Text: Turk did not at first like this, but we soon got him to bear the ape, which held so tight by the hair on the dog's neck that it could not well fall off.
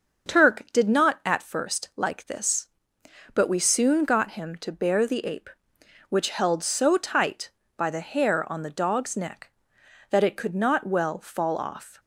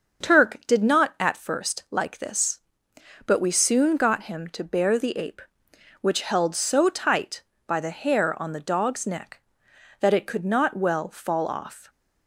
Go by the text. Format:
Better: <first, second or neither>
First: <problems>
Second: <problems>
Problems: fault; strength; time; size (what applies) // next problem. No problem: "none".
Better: neither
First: starts louder than the rest; until 1.3 s; 6.5 dB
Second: starts louder than the rest; until 1.3 s; 6.5 dB